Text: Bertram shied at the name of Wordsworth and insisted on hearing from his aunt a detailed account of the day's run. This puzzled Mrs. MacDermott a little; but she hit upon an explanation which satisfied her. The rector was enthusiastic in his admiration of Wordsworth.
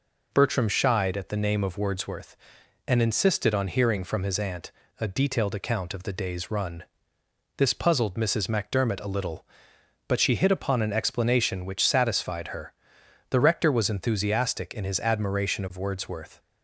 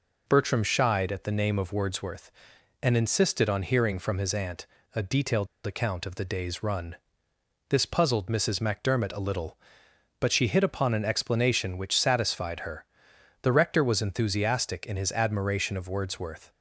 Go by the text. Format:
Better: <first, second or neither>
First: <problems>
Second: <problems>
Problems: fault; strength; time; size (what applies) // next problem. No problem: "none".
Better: first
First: pauses between "aunt" and "a"; slight; at 4.7 s; 0.28 s long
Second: pauses between "aunt" and "a"; slight; at 4.6 s; 0.28 s long // pauses between "detailed" and "account"; slight; at 5.4 s; 0.19 s long